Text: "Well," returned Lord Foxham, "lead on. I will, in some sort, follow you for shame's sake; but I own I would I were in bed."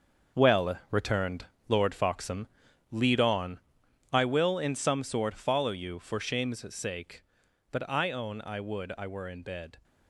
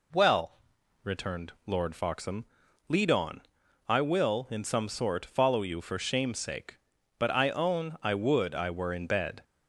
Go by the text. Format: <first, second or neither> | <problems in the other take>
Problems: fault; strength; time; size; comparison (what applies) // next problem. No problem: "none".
second | gets quieter; strong; throughout; 10.5 dB // pauses between "returned" and "Lord"; slight; at 1.4 s; 0.20 s long